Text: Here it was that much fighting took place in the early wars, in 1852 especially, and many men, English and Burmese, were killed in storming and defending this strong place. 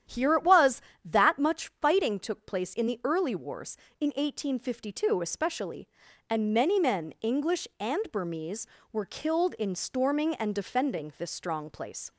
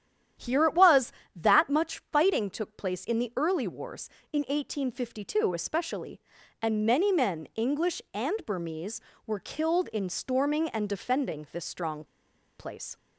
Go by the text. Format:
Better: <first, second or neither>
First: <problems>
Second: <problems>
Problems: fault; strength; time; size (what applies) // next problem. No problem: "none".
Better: first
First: starts louder than the rest; strong; until 1.3 s; 9.5 dB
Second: starts louder than the rest; strong; until 1.6 s; 9.5 dB // pauses between "strong" and "place"; noticeable; at 12.0 s; 0.54 s long